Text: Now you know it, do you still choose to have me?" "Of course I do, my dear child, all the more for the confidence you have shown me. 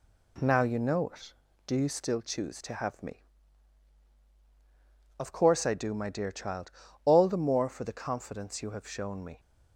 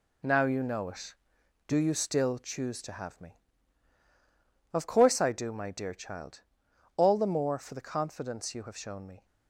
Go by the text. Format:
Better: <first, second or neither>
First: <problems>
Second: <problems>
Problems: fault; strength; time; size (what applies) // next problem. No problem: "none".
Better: first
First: none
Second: gets quieter; strong; throughout; 7 dB